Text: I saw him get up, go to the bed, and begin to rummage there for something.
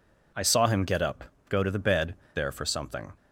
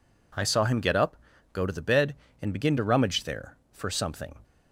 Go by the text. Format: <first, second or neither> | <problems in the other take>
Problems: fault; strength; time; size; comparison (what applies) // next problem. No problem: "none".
second | skips "and begin to rummage"; at 2.2 s